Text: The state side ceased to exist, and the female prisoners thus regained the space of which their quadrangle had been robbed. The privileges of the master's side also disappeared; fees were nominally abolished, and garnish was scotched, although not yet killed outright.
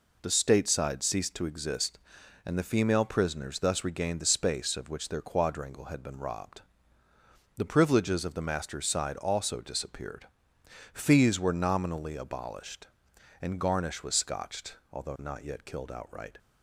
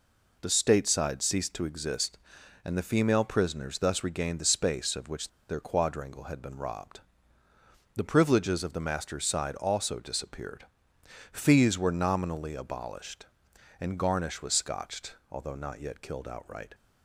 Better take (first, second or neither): first